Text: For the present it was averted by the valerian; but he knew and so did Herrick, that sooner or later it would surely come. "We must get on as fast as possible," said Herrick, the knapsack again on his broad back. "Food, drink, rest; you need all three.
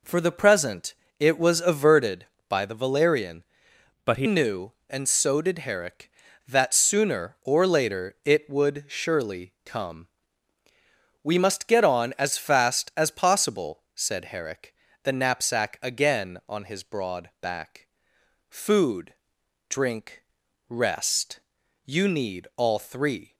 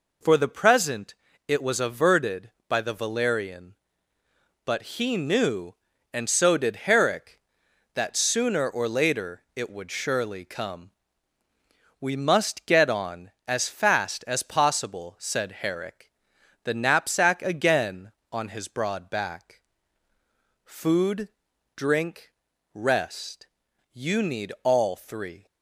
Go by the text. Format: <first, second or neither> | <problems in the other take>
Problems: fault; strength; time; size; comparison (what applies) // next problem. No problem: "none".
second | pauses between "present" and "it"; slight; at 0.9 s; 0.24 s long; slight in the second // changes voice from "but" to "he"; from 4.0 to 4.2 s; 0.2 s long